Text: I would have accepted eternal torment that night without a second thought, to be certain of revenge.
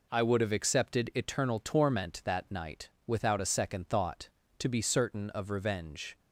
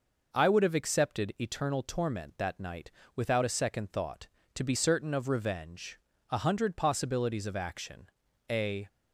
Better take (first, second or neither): first